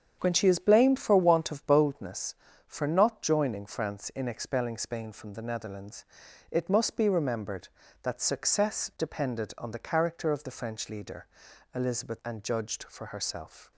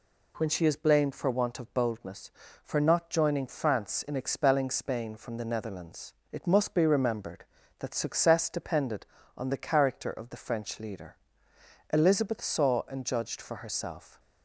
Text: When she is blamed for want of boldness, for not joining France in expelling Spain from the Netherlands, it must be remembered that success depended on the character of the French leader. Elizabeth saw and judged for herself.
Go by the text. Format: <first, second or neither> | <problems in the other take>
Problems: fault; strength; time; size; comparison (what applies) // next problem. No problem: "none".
second | starts louder than the rest; strong; until 1.2 s; 7.5 dB // skips "saw"; at 12.2 s